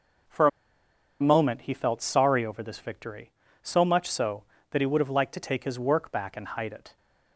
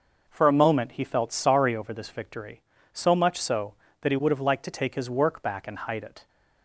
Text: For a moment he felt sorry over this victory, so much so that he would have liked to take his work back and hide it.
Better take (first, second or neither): second